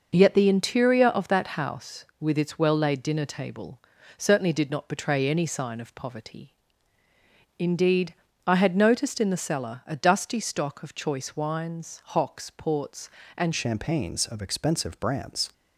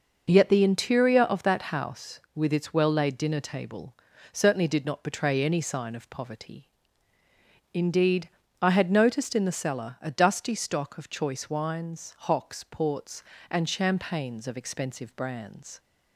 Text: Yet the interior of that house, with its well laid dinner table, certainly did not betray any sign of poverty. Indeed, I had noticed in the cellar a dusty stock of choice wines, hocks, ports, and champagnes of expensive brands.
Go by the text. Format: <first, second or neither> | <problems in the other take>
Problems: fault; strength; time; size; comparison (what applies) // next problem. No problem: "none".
second | changes voice at "champagnes"; from 13.5 s on; 2.0 s long